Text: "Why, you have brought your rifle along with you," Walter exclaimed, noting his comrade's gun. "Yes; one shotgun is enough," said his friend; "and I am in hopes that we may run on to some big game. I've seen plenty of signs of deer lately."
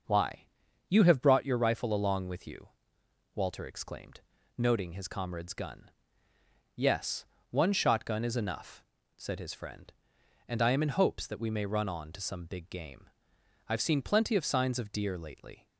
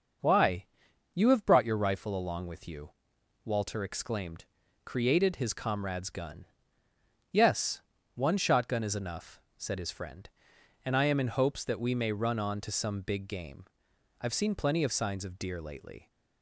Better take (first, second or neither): first